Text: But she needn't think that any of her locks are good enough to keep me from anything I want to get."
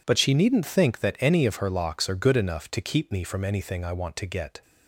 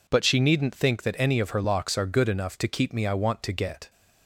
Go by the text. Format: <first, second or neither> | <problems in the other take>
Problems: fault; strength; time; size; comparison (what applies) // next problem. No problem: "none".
first | skips "from anything"; at 3.0 s